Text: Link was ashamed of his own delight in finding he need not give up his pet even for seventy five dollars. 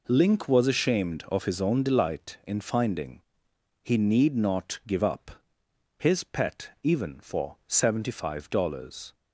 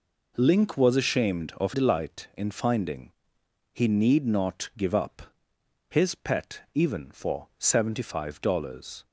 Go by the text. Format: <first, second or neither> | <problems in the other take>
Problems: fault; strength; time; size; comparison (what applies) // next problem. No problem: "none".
first | skips "his own"; at 1.7 s // pauses between "finding" and "he"; noticeable; at 3.1 s; 0.60 s long; noticeable in the first // pauses between "up" and "his"; noticeable; at 5.2 s; 0.68 s long; noticeable in the first